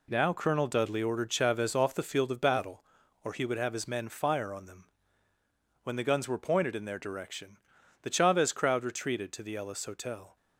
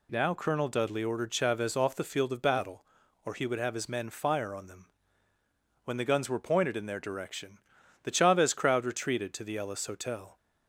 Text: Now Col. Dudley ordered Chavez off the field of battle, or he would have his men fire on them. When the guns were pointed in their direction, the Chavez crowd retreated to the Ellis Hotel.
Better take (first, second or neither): second